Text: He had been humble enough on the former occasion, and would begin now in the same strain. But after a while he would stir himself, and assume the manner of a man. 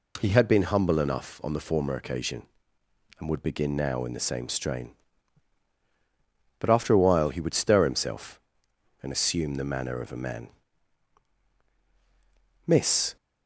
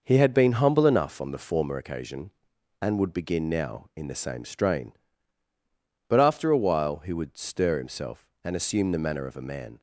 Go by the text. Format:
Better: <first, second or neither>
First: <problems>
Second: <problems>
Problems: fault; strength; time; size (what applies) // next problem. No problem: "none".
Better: second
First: goes on to say "Miss"; from 12.6 s on; 0.50 s long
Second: none